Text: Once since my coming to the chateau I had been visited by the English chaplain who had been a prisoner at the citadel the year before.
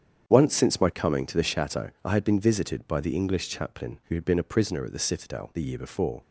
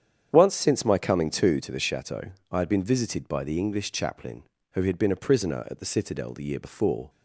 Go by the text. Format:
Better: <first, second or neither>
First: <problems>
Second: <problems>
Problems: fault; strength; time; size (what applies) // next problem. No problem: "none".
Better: first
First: starts louder than the rest; strong; until 1.3 s; 8.5 dB // pauses between "chateau" and "I"; slight; at 1.8 s; 0.16 s long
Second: starts louder than the rest; strong; until 1.3 s; 8.5 dB // says "to" twice; at 1.6 s // pauses between "chateau" and "I"; slight; at 2.2 s; 0.30 s long